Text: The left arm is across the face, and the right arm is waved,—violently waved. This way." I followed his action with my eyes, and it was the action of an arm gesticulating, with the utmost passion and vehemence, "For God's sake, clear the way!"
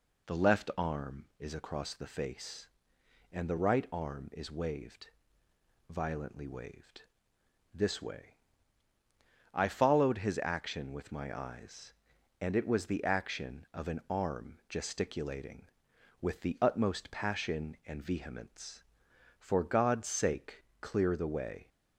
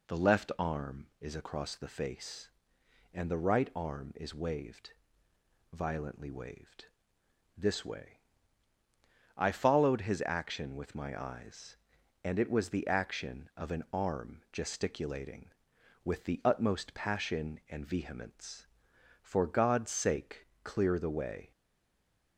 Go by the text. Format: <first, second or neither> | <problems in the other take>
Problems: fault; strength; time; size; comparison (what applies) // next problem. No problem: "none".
first | stays silent after the last word; slight; from 21.5 s on; 0.8 s long